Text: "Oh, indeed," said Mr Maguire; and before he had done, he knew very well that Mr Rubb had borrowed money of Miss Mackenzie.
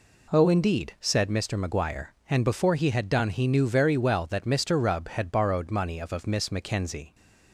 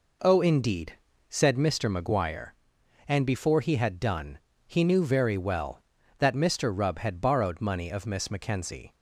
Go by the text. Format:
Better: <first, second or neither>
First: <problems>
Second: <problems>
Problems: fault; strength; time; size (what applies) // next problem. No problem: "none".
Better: second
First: says "of" twice; at 6.1 s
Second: none